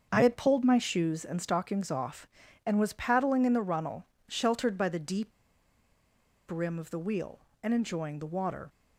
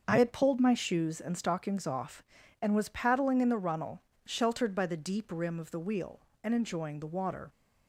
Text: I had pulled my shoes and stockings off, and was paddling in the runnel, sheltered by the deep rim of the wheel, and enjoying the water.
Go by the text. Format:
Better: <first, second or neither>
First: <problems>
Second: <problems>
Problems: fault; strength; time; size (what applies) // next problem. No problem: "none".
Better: second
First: starts louder than the rest; until 1.1 s; 7 dB // pauses between "deep" and "rim"; at 5.3 s; 1.1 s long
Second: starts louder than the rest; until 1.0 s; 6.5 dB